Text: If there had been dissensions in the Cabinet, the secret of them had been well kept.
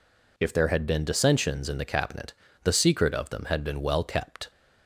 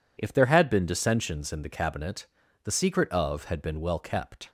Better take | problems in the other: first | skips "them"; at 3.4 s

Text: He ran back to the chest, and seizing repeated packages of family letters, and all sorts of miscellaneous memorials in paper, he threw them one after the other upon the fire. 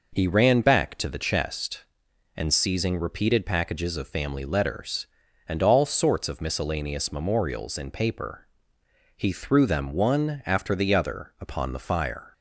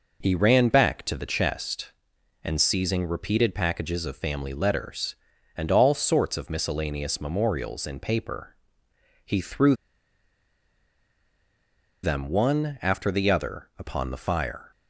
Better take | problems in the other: first | pauses between "threw" and "them"; strong; at 9.7 s; 2.3 s long

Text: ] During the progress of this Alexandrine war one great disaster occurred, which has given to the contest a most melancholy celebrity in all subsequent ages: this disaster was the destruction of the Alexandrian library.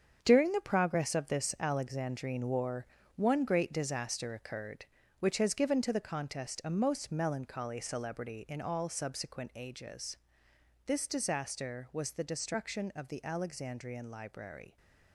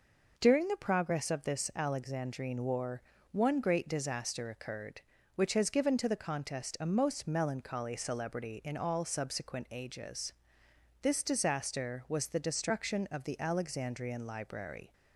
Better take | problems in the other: second | gets quieter; strong; throughout; 9.5 dB // pauses between "war" and "one"; slight; at 2.8 s; 0.32 s long; slight in the second

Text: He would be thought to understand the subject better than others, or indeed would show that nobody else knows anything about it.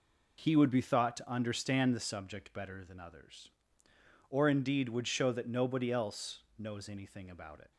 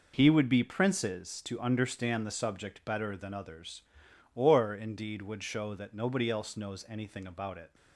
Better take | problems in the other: first | says "princes" for "thought"; at 0.6 s

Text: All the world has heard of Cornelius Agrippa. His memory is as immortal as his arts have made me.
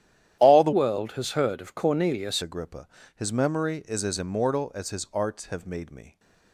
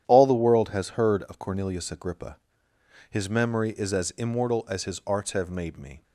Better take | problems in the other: second | starts louder than the rest; strong; until 1.3 s; 11.5 dB; strong in the second // changes voice from "world" to "Cornelius"; from 0.7 to 2.4 s; 1.7 s long

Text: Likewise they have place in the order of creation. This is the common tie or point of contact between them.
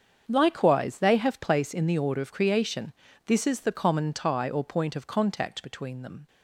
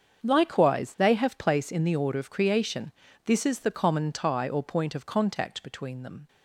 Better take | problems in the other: neither | starts louder than the rest; the same in both

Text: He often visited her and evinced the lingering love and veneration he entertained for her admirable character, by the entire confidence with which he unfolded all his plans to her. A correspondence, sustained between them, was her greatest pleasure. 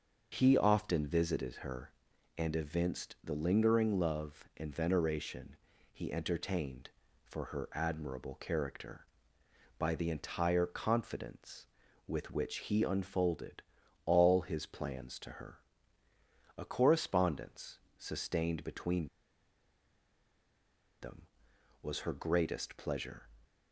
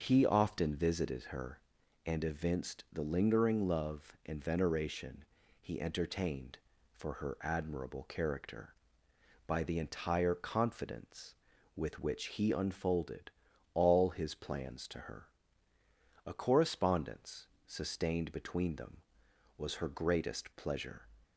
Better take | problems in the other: second | starts louder than the rest; until 1.3 s; 6.5 dB; also in the second // pauses between "veneration" and "he"; slight; at 5.5 s; 0.36 s long; slight in the second // pauses between "unfolded" and "all"; noticeable; at 13.6 s; 0.46 s long; noticeable in the second // pauses between "between" and "them"; strong; at 19.0 s; 1.9 s long

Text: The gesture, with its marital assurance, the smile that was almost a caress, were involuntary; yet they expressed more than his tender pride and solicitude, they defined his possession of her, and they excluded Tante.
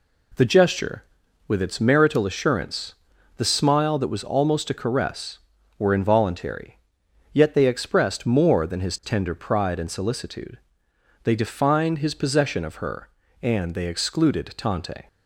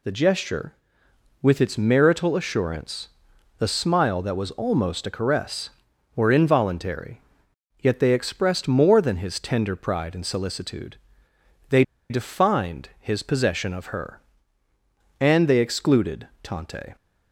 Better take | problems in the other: first | pauses between "they" and "defined"; slight; at 11.8 s; 0.27 s long

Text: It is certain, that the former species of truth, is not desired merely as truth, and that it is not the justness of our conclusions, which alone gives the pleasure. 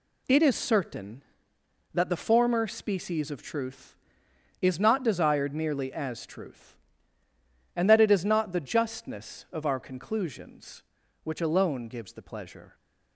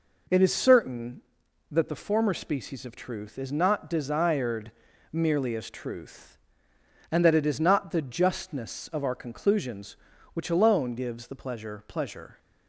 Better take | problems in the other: first | pauses between "desired" and "merely"; at 4.7 s; 0.40 s long // says "pleasure" twice; at 11.8 s

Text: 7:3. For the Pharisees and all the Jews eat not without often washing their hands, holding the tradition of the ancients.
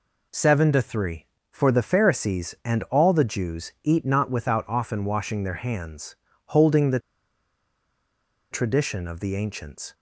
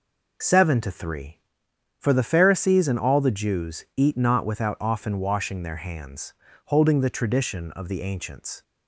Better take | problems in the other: second | pauses between "the" and "tradition"; strong; at 6.9 s; 1.5 s long

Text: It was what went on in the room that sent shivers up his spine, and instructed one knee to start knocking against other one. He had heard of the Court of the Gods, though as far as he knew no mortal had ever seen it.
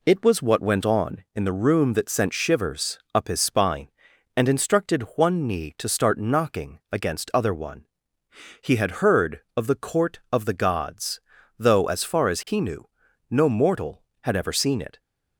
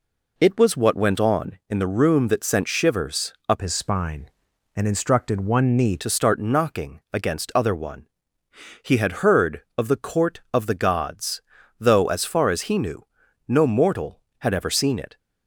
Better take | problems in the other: first | pauses between "shivers" and "up"; slight; at 3.3 s; 0.16 s long; slight in the first // changes voice from "his" to "knee"; from 3.6 to 5.9 s; 2.3 s long // pauses between "knew" and "no"; at 13.0 s; 0.44 s long; also in the first

